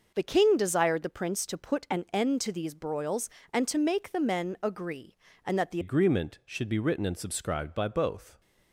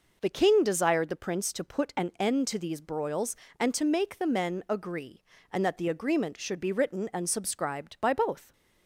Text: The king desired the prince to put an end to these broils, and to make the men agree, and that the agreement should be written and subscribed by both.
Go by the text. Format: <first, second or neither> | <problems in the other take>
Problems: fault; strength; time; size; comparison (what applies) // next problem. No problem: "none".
second | changes voice at "agreement"; from 5.8 s on; 2.6 s long